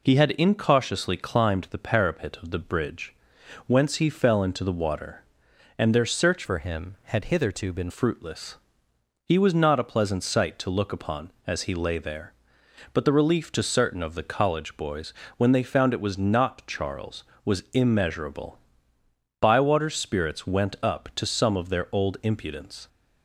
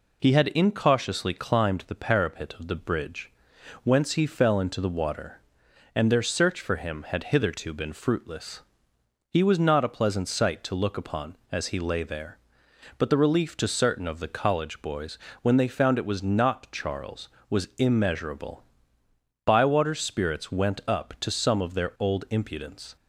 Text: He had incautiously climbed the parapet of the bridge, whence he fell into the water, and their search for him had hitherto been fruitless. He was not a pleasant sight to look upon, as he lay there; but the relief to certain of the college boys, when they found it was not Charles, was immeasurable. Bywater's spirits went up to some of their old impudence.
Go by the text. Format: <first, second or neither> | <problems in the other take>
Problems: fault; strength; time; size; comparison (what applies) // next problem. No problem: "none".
second | changes voice from "for" to "been"; from 6.4 to 7.8 s; 1.4 s long